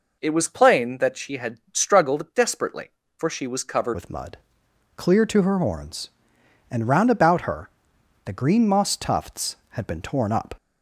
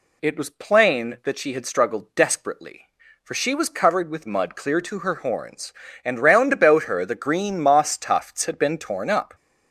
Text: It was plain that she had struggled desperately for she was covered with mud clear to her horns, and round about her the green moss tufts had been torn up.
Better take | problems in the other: second | changes voice at "with"; from 3.9 s on; 6.6 s long // pauses between "mud" and "clear"; noticeable; at 4.3 s; 0.58 s long // pauses between "her" and "the"; noticeable; at 7.6 s; 0.56 s long

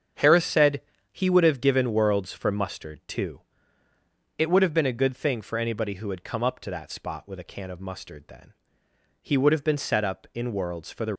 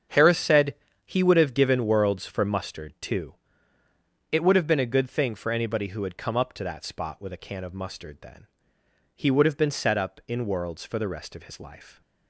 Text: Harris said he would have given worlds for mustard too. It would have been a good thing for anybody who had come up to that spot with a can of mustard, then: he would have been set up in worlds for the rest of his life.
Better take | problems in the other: second | starts louder than the rest; strong; until 1.4 s; 7.5 dB; strong in the second // pauses between "said" and "he"; slight; at 0.8 s; 0.30 s long; slight in the second // stops before "rest of his life"; at 11.1 s

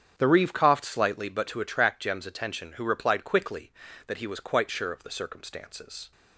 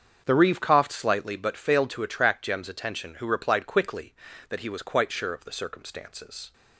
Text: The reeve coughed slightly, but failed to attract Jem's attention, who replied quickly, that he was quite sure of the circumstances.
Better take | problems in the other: second | starts louder than the rest; strong; until 1.1 s; 8.5 dB; also in the second // skips "failed"; at 1.4 s

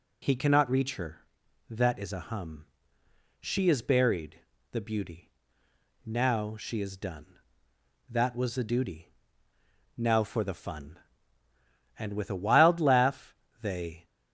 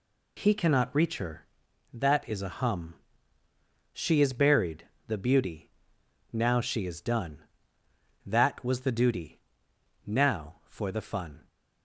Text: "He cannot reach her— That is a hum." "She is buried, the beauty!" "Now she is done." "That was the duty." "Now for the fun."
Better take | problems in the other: second | goes on to say "And with a wild laugh they"; strong; from 11.9 s on; 2.0 s long

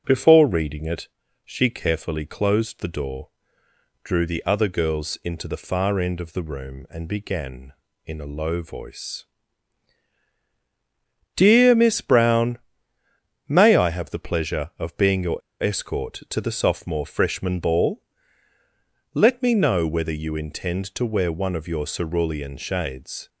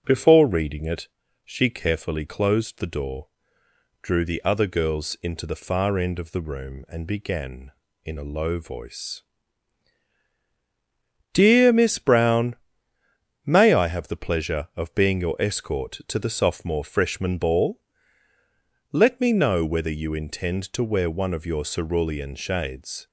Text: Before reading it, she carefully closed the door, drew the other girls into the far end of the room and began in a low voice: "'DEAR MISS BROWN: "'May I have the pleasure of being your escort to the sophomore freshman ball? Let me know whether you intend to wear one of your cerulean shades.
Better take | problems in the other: second | starts louder than the rest; noticeable; until 1.0 s; 6 dB // pauses between "your" and "escort"; slight; at 15.4 s; 0.21 s long

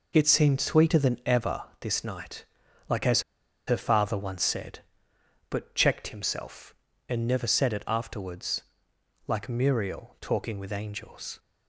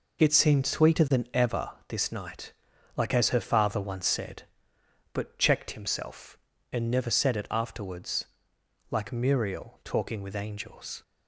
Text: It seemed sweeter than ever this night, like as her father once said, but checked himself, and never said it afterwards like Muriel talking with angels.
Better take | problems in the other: second | pauses between "ever" and "this"; slight; at 1.6 s; 0.16 s long; slight in the second // pauses between "as" and "her"; at 3.2 s; 0.45 s long // pauses between "afterwards" and "like"; noticeable; at 8.6 s; 0.66 s long; noticeable in the second

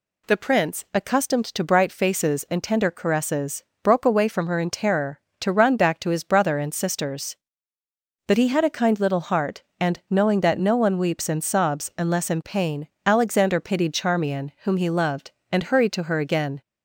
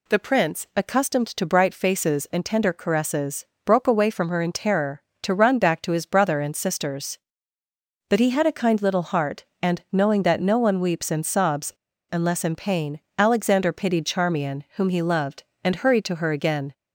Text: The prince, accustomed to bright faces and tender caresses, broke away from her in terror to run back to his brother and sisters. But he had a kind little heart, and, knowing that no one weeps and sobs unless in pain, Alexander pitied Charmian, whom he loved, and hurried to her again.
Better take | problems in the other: first | pauses between "sobs" and "unless"; at 11.7 s; 0.38 s long

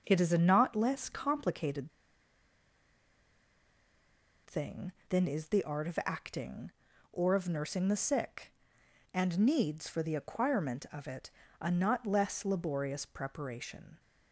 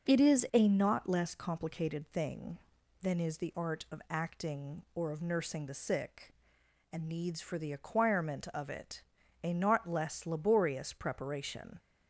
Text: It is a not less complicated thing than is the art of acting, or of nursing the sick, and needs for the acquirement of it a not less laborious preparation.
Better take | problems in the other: second | starts louder than the rest; noticeable; until 1.0 s; 6 dB // pauses between "complicated" and "thing"; strong; at 1.9 s; 2.5 s long // pauses between "it" and "a"; slight; at 11.2 s; 0.32 s long; also in the second

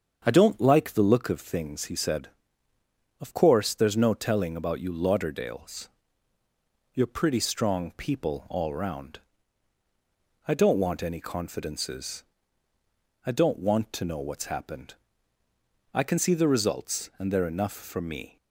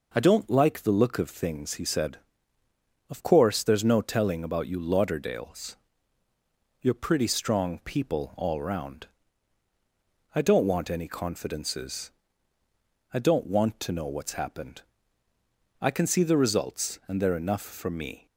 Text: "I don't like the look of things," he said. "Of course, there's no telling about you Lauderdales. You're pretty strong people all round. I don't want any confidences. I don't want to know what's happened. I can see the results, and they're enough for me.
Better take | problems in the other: second | starts louder than the rest; strong; until 1.3 s; 7 dB

